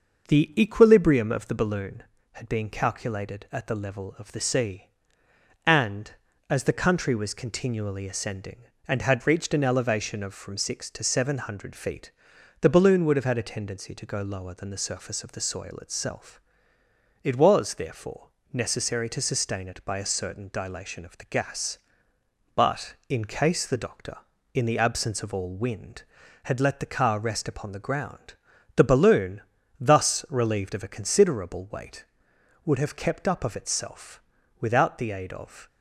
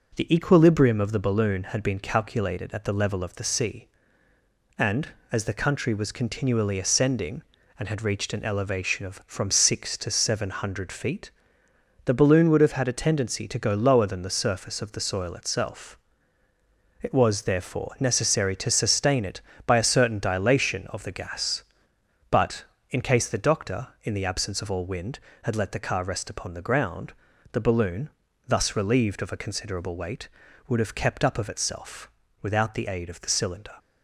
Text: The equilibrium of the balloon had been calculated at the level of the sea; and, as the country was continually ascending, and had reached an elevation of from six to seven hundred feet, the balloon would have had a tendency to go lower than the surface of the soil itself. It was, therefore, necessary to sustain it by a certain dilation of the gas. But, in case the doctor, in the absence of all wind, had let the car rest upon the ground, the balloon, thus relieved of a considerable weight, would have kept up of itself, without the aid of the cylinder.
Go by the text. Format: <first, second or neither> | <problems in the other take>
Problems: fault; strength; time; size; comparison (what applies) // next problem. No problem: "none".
second | stops before "the cylinder"; at 35.6 s